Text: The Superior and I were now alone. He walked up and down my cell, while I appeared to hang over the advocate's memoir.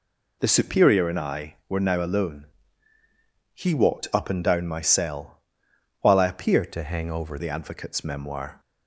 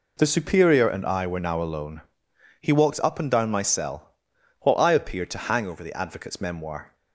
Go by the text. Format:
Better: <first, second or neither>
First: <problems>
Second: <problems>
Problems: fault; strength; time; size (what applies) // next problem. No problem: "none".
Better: second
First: changes voice from "to" to "over"; from 6.7 to 7.3 s; 0.6 s long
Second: none